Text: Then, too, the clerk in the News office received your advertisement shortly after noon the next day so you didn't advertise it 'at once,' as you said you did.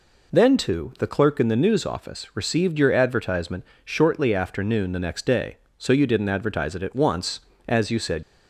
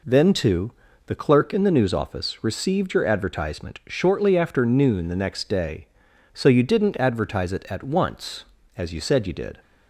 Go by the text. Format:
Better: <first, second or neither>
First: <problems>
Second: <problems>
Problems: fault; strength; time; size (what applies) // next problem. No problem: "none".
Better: second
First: pauses between "advertisement" and "shortly"; slight; at 3.6 s; 0.20 s long // stops before "you did"; at 8.2 s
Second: none